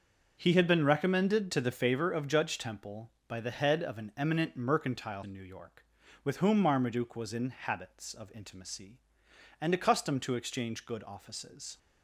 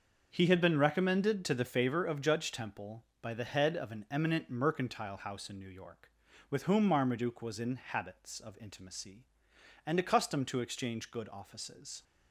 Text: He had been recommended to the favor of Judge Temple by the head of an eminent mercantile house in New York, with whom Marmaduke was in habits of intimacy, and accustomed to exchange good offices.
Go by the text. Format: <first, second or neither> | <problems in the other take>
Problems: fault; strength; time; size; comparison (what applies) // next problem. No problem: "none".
second | starts louder than the rest; until 1.3 s; 6.5 dB; also in the second // skips "house"; at 5.2 s